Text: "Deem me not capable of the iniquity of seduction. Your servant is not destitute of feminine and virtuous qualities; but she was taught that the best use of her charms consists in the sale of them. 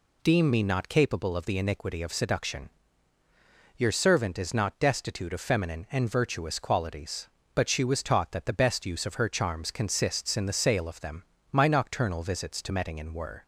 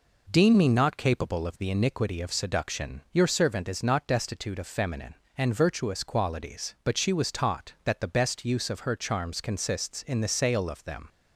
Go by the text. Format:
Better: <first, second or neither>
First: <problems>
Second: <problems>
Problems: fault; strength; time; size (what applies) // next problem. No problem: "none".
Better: second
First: goes on to say "My nocturnal visits to Mettingen were"; strong; from 11.5 s on; 1.9 s long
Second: none